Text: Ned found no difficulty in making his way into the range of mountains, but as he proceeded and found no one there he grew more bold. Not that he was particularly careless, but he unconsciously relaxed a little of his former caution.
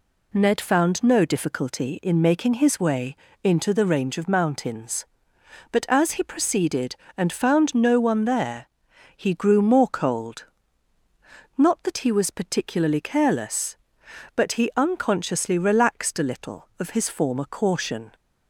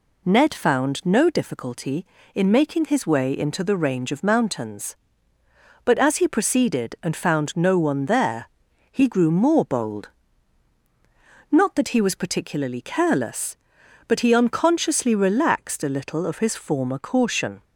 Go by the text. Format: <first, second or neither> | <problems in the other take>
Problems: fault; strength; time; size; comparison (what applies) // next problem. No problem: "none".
second | pauses between "way" and "into"; slight; at 3.1 s; 0.28 s long // pauses between "there" and "he"; noticeable; at 8.6 s; 0.48 s long; also in the second // says "cold" for "bold"; at 9.8 s